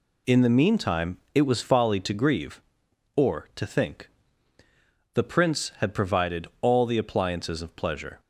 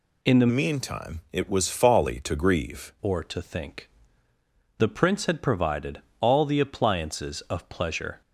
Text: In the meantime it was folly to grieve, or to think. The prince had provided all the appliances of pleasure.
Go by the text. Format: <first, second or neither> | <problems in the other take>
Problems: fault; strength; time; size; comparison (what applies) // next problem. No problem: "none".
first | changes voice from "meantime" to "grieve"; from 0.5 to 2.9 s; 2.4 s long // pauses between "provided" and "all"; slight; at 6.0 s; 0.20 s long